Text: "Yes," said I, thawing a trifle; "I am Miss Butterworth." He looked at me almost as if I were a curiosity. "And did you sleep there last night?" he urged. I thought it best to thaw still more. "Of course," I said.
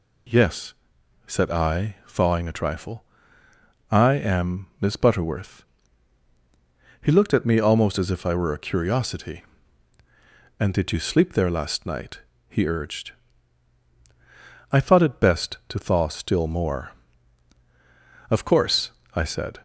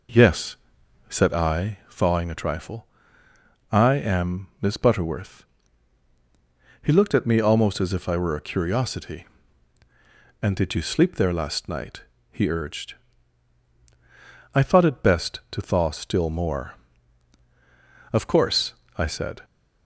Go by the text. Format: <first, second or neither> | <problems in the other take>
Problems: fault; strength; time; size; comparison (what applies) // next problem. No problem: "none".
first | starts louder than the rest; noticeable; until 1.5 s; 4.5 dB